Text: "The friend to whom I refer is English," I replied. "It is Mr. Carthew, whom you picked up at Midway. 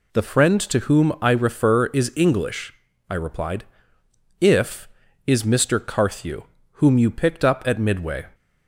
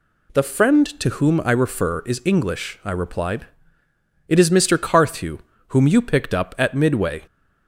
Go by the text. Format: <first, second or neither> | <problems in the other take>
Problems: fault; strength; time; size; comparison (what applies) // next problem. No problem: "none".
second | says "If" for "It"; at 4.4 s